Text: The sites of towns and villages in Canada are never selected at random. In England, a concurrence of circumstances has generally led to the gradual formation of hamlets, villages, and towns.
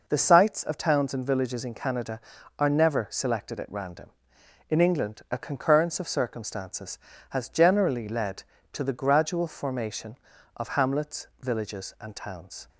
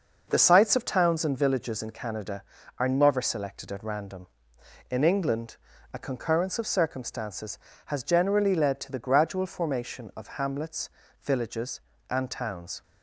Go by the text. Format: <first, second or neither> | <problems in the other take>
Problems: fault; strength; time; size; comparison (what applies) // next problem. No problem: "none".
neither | none